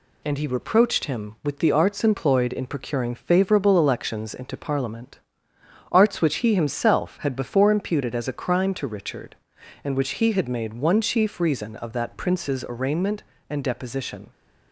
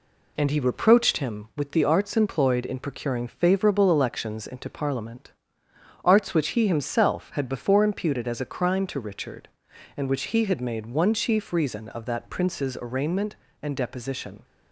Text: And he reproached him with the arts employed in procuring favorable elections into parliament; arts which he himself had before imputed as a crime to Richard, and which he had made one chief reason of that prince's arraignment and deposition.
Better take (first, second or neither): first